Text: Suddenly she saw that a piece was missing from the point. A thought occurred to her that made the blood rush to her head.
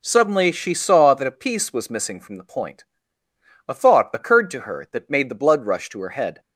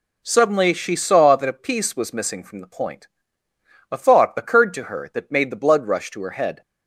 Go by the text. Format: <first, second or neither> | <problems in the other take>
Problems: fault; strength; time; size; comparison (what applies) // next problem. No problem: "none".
neither | none